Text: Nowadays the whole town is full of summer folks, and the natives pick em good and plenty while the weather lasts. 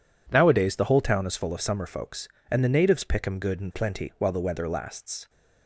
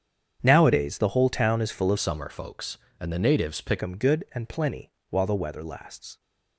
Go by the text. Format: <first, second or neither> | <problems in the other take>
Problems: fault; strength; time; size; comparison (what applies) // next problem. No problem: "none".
first | starts louder than the rest; strong; until 1.4 s; 8 dB // changes voice from "summer" to "pick"; from 1.9 to 3.8 s; 1.9 s long // pauses between "plenty" and "while"; slight; at 4.8 s; 0.20 s long